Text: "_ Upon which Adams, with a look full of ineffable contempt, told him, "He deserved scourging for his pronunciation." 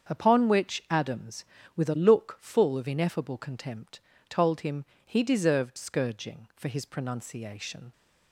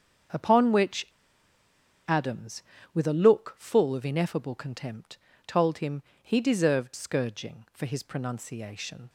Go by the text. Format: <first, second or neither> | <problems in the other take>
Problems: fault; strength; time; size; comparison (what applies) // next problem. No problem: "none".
first | starts louder than the rest; strong; until 2.3 s; 7.5 dB; strong in the first // pauses between "which" and "Adams"; at 1.0 s; 1.0 s long